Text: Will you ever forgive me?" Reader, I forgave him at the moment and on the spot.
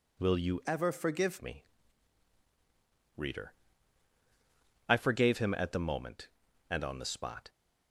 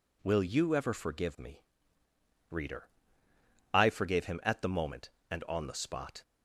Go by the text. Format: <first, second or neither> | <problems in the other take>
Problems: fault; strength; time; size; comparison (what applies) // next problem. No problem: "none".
second | changes voice from "ever" to "forgive"; from 0.6 to 1.3 s; 0.7 s long